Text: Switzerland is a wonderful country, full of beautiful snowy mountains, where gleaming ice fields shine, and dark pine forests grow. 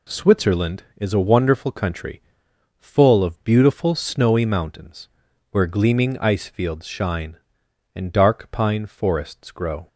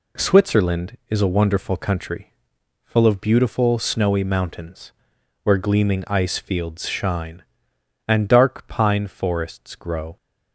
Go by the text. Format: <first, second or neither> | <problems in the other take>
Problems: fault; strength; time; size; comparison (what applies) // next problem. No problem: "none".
neither | none